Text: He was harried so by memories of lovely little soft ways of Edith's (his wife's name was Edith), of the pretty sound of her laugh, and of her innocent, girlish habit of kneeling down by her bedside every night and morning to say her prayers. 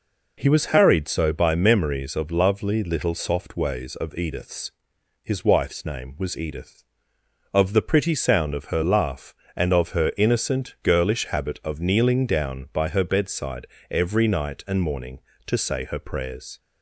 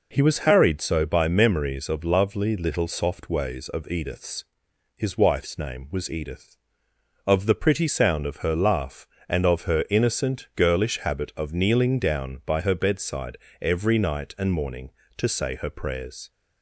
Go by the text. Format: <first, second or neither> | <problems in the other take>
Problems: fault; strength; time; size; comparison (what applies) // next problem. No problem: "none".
neither | pauses between "bedside" and "every"; slight; the same in both